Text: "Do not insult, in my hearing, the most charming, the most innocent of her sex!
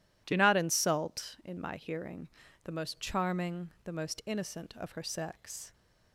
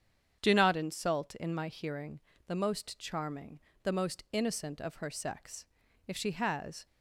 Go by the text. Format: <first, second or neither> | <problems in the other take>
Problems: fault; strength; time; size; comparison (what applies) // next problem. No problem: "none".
first | starts louder than the rest; strong; until 1.4 s; 8 dB // goes on to say "If she has"; noticeable; from 6.0 s on; 0.80 s long